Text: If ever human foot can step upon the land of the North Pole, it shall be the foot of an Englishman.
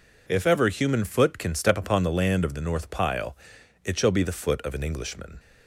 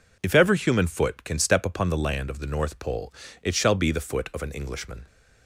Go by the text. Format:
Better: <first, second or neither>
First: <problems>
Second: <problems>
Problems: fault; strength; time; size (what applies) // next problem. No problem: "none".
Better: second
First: says "Pile" for "Pole"; at 2.8 s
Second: none